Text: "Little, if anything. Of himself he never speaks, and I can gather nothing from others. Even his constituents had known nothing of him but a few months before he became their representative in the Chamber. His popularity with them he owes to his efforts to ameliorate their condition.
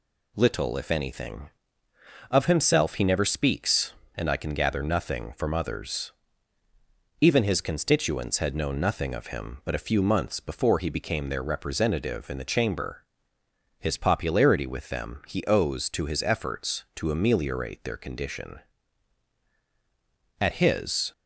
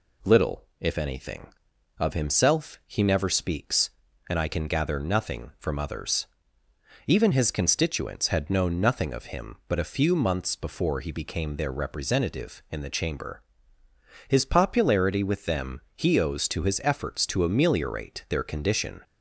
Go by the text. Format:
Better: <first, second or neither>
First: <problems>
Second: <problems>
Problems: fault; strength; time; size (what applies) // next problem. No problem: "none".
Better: second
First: goes on to say "At his"; noticeable; from 20.3 s on; 0.72 s long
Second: none